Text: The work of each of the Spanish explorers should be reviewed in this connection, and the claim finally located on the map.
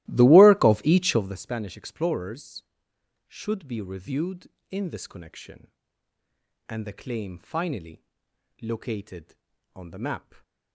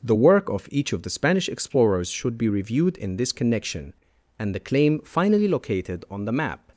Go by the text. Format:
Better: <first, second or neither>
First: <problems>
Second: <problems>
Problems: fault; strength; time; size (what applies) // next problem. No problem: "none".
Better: second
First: starts louder than the rest; strong; until 1.4 s; 16.5 dB // pauses between "finally" and "located"; noticeable; at 8.0 s; 0.58 s long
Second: none